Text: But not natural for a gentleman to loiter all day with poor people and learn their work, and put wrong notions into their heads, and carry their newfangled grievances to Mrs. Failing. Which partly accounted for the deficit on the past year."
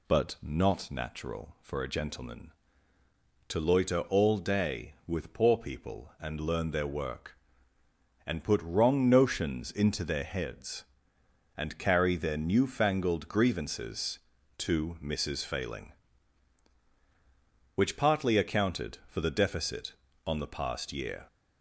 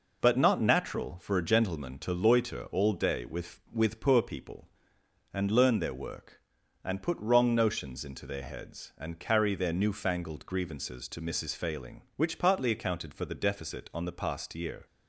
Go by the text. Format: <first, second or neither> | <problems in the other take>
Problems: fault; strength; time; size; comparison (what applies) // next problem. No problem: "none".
first | says "with" twice; at 3.7 s